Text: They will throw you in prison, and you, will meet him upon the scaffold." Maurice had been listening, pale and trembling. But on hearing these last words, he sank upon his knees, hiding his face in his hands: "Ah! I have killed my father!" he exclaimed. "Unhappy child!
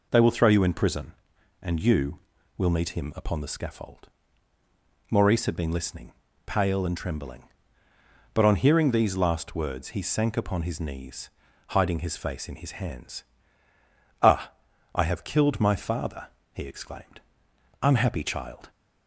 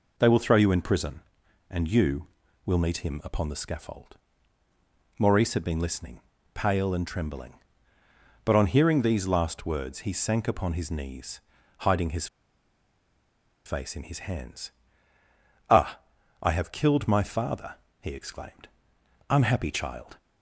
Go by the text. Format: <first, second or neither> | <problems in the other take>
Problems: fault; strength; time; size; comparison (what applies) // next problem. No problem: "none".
first | pauses between "his" and "face"; strong; at 12.2 s; 1.3 s long